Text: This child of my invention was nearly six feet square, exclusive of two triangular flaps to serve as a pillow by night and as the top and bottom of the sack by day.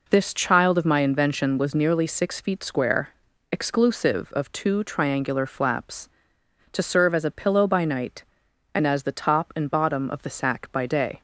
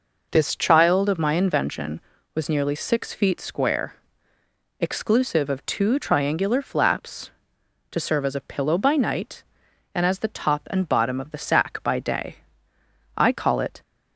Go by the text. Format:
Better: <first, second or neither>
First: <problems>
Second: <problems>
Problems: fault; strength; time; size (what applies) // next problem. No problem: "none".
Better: first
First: none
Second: goes on to say "I call it"; noticeable; from 13.1 s on; 0.66 s long